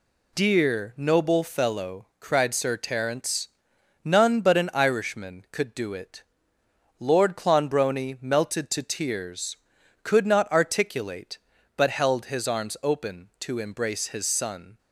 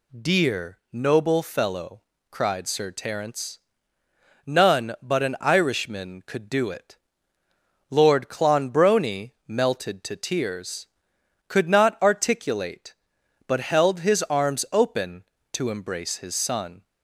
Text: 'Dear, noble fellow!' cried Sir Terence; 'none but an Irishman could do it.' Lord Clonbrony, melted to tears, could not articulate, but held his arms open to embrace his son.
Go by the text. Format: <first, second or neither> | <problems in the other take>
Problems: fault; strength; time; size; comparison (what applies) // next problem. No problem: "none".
neither | none